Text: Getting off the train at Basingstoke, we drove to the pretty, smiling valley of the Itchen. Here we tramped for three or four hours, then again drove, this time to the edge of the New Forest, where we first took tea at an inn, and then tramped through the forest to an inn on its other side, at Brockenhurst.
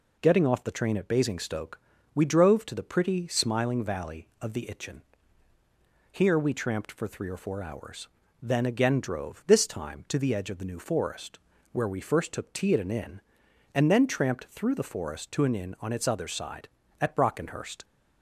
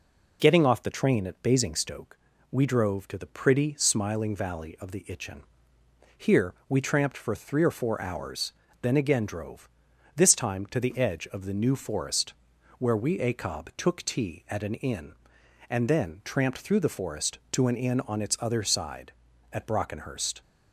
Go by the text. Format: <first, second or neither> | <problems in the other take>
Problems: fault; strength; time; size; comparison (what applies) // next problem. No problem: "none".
first | says "acob" for "first"; at 13.1 s